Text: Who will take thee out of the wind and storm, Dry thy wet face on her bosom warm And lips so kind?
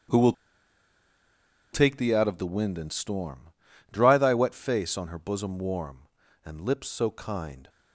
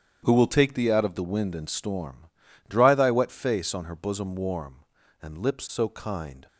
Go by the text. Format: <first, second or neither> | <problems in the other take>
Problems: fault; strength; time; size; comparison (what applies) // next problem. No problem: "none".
second | starts louder than the rest; strong; until 2.4 s; 9 dB; strong in the second // pauses between "will" and "take"; strong; at 0.3 s; 1.3 s long